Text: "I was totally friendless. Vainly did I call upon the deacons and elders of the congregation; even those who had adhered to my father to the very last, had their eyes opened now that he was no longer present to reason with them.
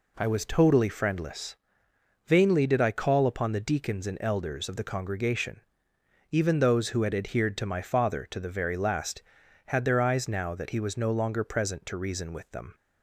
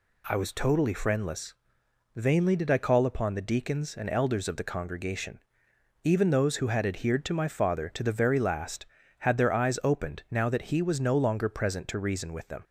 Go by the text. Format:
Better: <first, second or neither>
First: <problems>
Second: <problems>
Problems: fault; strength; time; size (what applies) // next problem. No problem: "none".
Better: second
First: skips "opened"; at 10.2 s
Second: none